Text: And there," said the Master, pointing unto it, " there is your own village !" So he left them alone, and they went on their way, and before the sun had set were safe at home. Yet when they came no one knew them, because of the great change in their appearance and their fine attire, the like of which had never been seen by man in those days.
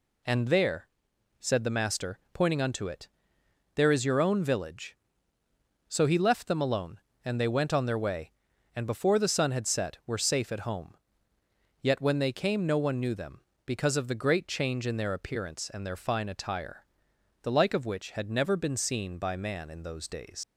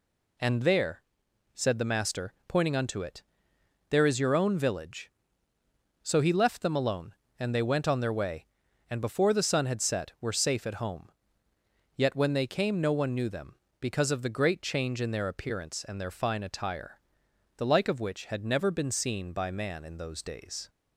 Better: second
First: leaves "days" unfinished; at 20.4 s; 110 ms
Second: none

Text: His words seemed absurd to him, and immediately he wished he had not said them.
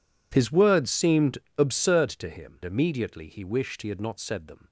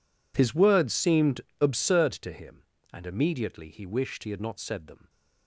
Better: second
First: pauses between "seemed" and "absurd"; slight; at 1.3 s; 0.22 s long // skips "and"; at 2.6 s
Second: pauses between "seemed" and "absurd"; slight; at 1.3 s; 0.22 s long

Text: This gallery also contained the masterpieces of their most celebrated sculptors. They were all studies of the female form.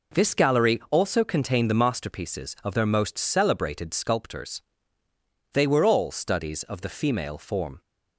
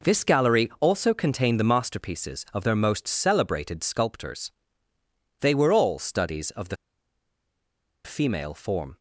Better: first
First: none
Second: pauses between "the" and "female"; strong; at 6.7 s; 1.2 s long

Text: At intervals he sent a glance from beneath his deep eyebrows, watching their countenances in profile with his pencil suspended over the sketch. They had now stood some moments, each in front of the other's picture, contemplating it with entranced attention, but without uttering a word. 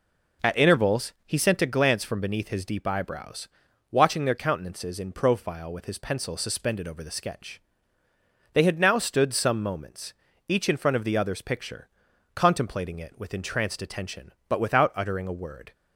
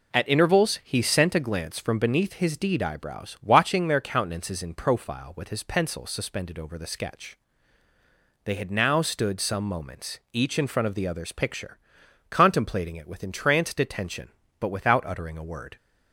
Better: first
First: none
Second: says "deed" for "deep"; at 2.5 s

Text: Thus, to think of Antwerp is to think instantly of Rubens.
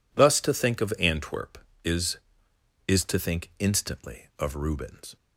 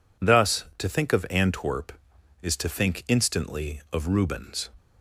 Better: second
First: says "is" twice; at 2.8 s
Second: none

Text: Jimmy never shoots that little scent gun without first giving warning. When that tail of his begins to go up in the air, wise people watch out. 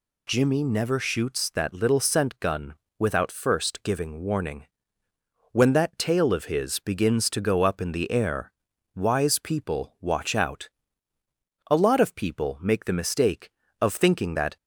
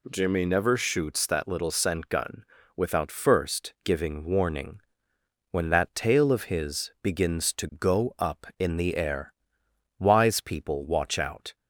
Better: second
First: pauses between "gun" and "without"; slight; at 2.7 s; 0.24 s long // goes on to say "A lot of people make the mistake of thinking that"; strong; from 11.7 s on; 2.8 s long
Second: pauses between "gun" and "without"; slight; at 2.4 s; 0.32 s long

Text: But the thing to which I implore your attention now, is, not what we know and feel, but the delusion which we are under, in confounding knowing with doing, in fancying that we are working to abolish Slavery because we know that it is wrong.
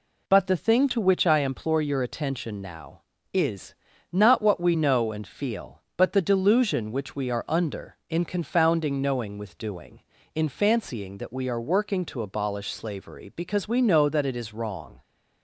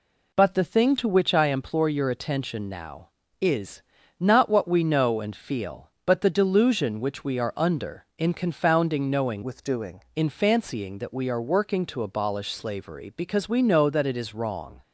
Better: first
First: none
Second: changes voice from "with" to "doing"; from 9.4 to 10.0 s; 0.6 s long

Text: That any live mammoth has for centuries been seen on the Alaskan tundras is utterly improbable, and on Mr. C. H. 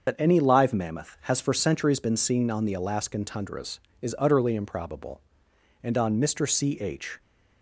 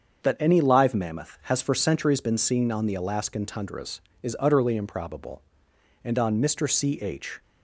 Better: second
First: loses the start of "That"; at 0.0 s; 60 ms // starts louder than the rest; until 1.1 s; 6.5 dB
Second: starts louder than the rest; until 1.2 s; 7 dB

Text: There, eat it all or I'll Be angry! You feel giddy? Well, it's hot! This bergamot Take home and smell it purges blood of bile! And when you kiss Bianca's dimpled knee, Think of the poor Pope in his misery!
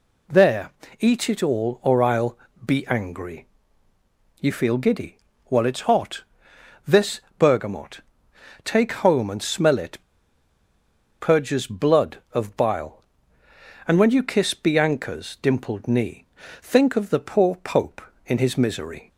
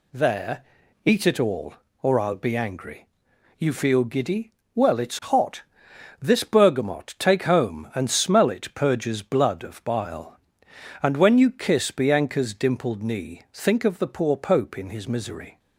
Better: second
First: pauses between "I'll" and "Be"; slight; at 2.3 s; 0.28 s long // pauses between "This" and "bergamot"; slight; at 7.2 s; 0.18 s long // pauses between "bergamot" and "Take"; noticeable; at 8.0 s; 0.64 s long // pauses between "it" and "purges"; at 9.9 s; 1.2 s long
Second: none

